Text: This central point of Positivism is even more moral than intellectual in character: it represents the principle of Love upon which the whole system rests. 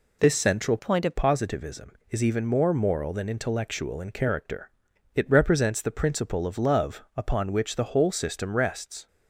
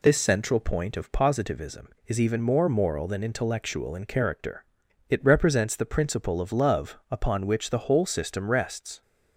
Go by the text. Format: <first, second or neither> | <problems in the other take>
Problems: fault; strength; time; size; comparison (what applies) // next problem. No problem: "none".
second | changes voice from "point" to "of"; from 0.7 to 1.1 s; 0.4 s long